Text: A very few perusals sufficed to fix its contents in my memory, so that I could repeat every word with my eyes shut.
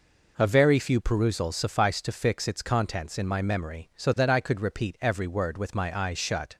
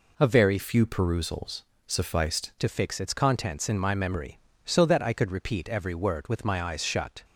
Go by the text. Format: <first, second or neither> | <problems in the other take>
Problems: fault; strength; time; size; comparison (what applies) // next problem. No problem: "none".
first | changes voice from "few" to "sufficed"; from 0.5 to 2.4 s; 1.9 s long // pauses between "perusals" and "sufficed"; slight; at 1.6 s; 0.24 s long